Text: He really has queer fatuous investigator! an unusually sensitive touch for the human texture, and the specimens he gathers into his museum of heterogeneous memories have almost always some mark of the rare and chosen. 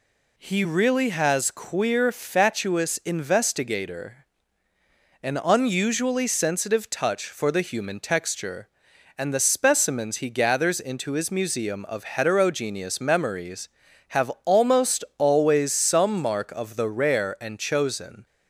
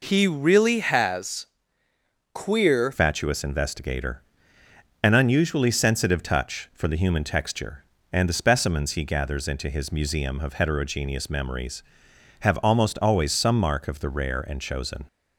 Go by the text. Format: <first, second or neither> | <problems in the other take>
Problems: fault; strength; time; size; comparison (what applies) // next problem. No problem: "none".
first | pauses between "has" and "queer"; noticeable; at 1.4 s; 0.88 s long // changes voice at "fatuous"; from 2.9 s on; 12.1 s long